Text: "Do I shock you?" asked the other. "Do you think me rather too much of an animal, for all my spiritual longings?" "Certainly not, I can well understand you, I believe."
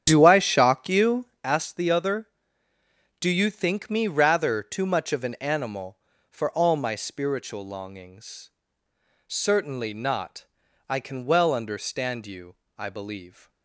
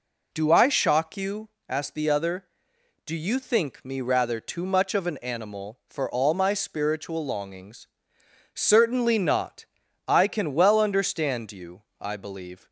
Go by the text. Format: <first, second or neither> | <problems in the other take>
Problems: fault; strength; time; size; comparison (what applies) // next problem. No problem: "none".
second | starts louder than the rest; strong; until 1.5 s; 9 dB